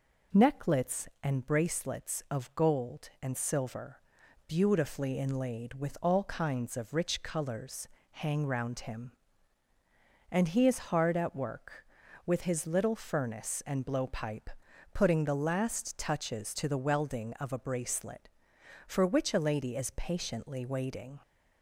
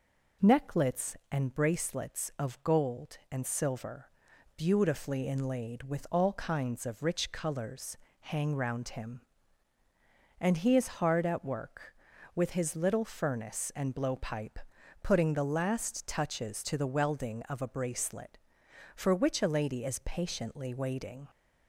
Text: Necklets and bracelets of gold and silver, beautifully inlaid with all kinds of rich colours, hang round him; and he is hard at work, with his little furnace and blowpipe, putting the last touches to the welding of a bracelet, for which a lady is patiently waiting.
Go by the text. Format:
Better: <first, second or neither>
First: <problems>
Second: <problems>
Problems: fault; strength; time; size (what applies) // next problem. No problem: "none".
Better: neither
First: none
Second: none